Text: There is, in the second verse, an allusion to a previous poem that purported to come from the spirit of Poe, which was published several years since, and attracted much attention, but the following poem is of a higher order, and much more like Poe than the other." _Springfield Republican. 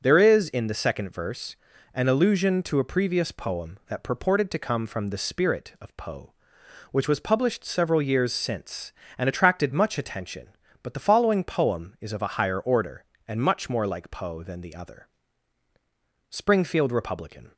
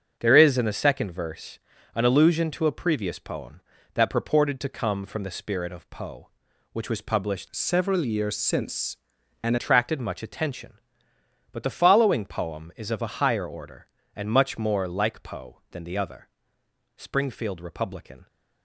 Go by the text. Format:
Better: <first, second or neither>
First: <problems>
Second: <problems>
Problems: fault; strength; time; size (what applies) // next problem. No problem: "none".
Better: first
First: starts louder than the rest; until 1.0 s; 6.5 dB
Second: starts louder than the rest; until 1.2 s; 6.5 dB // changes voice from "several" to "and"; from 7.5 to 9.5 s; 2.0 s long